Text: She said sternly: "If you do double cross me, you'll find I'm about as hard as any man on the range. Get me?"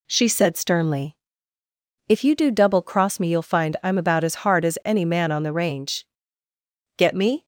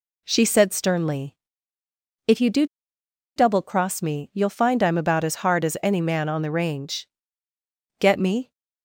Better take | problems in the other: first | pauses between "do" and "double"; noticeable; at 2.6 s; 0.70 s long

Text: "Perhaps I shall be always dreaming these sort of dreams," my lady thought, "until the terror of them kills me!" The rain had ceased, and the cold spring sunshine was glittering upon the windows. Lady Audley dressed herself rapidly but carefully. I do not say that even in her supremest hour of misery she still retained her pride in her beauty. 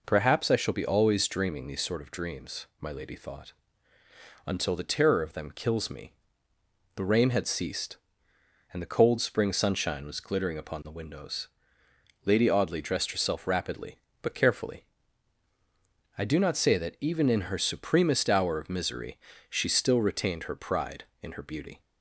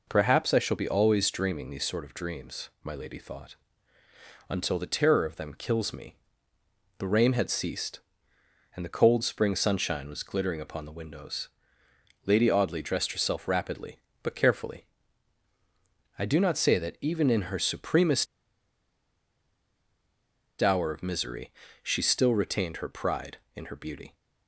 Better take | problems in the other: first | pauses between "supremest" and "hour"; strong; at 18.2 s; 2.3 s long // pauses between "misery" and "she"; slight; at 21.5 s; 0.30 s long; slight in the first

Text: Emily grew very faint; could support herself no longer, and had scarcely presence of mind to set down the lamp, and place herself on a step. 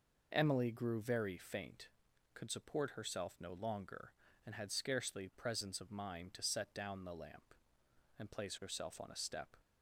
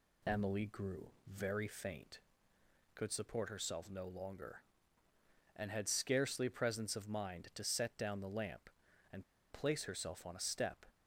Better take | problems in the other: first | pauses between "grew" and "very"; slight; at 1.1 s; 0.16 s long // pauses between "and" and "place"; slight; at 9.2 s; 0.28 s long

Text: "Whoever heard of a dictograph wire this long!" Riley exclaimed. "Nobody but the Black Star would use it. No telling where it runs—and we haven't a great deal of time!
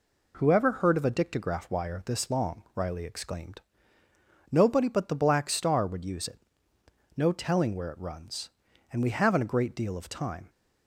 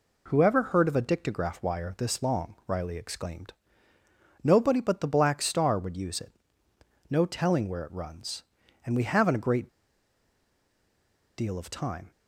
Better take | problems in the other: first | pauses between "great" and "deal"; strong; at 9.6 s; 1.6 s long

